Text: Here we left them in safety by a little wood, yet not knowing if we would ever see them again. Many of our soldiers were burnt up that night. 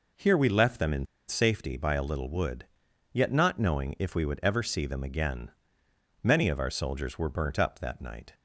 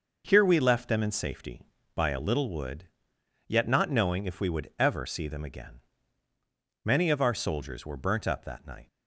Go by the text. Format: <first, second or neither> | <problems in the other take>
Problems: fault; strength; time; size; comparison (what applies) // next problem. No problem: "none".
second | pauses between "in" and "safety"; slight; at 1.0 s; 0.23 s long